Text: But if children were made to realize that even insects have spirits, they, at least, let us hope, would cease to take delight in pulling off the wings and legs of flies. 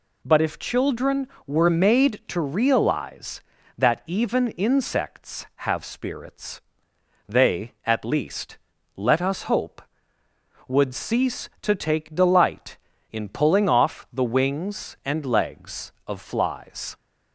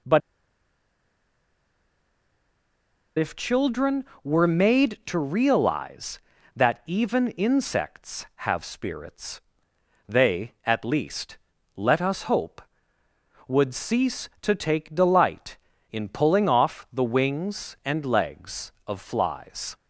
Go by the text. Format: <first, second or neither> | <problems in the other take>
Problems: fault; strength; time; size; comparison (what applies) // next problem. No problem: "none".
first | pauses between "But" and "if"; strong; at 0.2 s; 2.9 s long